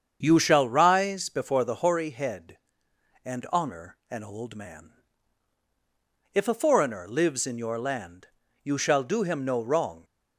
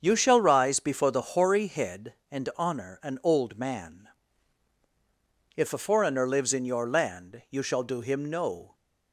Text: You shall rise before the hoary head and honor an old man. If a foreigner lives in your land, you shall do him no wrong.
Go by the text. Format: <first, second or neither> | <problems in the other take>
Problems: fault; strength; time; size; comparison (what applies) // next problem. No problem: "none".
first | starts louder than the rest; until 1.0 s; 7 dB; strong in the first // stops before "wrong"; at 8.7 s